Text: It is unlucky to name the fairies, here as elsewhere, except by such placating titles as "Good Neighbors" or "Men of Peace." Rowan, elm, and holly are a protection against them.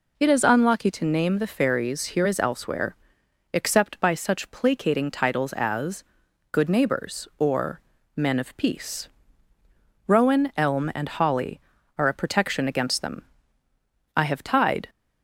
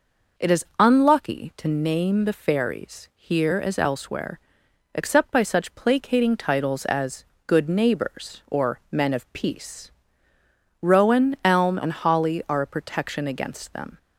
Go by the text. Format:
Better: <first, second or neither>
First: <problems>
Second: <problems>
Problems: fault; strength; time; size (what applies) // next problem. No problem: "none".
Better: second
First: pauses between "as" and "Good"; noticeable; at 6.0 s; 0.48 s long // pauses between "or" and "Men"; slight; at 7.8 s; 0.34 s long // goes on to say "I have tied"; noticeable; from 14.1 s on; 0.74 s long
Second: pauses between "as" and "Good"; slight; at 7.2 s; 0.24 s long